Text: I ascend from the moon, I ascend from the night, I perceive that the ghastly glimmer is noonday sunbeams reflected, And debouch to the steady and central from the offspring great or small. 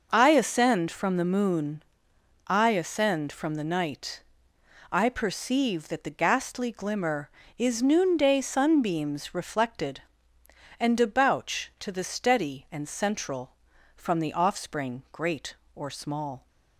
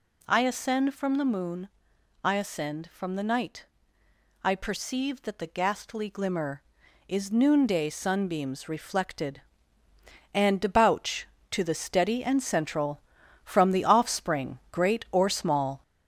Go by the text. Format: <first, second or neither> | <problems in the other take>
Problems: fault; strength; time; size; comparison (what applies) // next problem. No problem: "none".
first | gets louder; slight; throughout; 2.5 dB